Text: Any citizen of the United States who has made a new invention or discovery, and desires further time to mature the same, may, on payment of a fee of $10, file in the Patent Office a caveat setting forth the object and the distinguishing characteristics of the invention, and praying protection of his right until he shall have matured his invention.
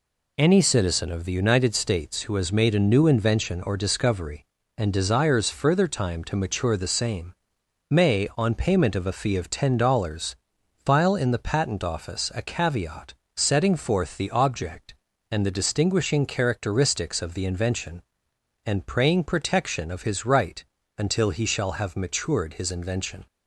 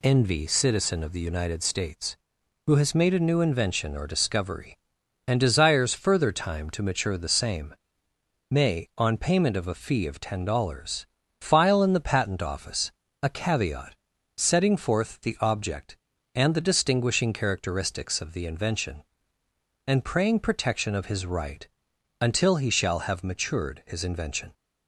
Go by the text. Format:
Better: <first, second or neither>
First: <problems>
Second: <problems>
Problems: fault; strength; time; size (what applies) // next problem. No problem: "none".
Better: first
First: pauses between "caveat" and "setting"; slight; at 13.1 s; 0.24 s long // pauses between "right" and "until"; slight; at 20.6 s; 0.32 s long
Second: says "Envy" for "Any"; at 0.0 s // pauses between "Office" and "a"; slight; at 12.8 s; 0.32 s long // pauses between "caveat" and "setting"; at 13.9 s; 0.42 s long // pauses between "right" and "until"; noticeable; at 21.6 s; 0.52 s long